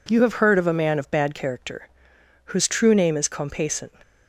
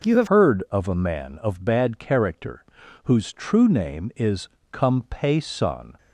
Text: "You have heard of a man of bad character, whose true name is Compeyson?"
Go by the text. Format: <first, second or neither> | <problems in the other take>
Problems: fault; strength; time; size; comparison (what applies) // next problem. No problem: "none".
first | changes voice at "heard"; from 0.2 s on; 5.7 s long // pauses between "is" and "Compeyson"; slight; at 4.4 s; 0.24 s long